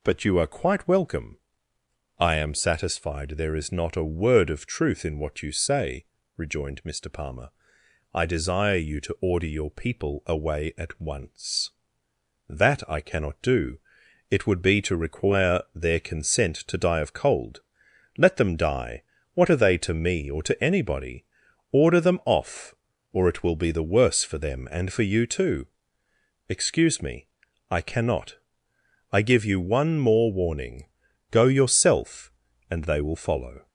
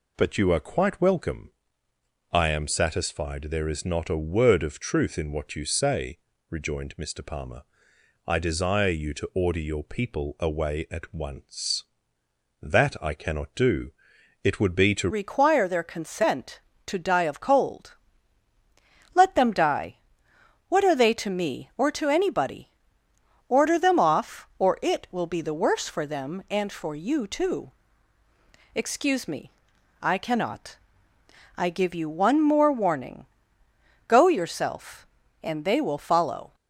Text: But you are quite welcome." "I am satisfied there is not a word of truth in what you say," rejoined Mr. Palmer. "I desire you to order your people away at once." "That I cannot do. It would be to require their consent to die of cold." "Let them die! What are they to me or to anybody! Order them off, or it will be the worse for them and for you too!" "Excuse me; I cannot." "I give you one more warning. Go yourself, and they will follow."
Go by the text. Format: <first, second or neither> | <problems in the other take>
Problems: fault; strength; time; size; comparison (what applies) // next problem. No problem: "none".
first | changes voice at "require"; from 15.0 s on; 21.5 s long